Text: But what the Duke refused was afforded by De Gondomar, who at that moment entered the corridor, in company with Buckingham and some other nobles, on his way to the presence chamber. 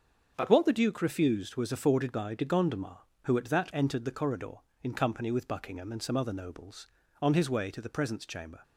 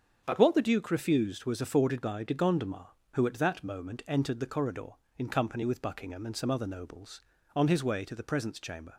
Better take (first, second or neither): second